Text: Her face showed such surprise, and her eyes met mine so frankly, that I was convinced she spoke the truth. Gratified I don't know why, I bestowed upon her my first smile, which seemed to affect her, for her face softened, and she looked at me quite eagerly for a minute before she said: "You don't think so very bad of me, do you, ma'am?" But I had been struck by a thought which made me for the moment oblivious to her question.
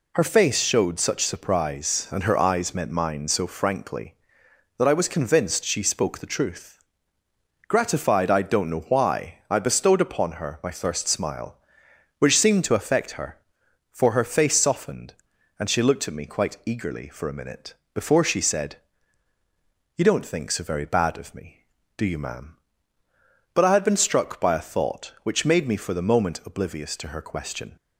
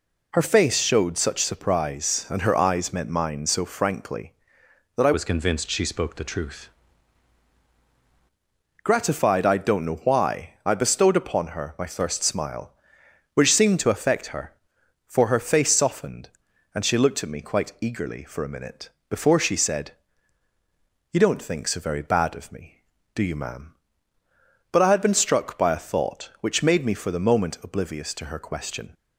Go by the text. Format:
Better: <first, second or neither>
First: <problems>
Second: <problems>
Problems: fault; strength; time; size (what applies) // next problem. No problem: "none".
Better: first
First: pauses between "minute" and "before"; slight; at 17.7 s; 0.22 s long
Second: changes voice from "was" to "truth"; from 5.1 to 6.6 s; 1.5 s long // pauses between "minute" and "before"; slight; at 18.8 s; 0.22 s long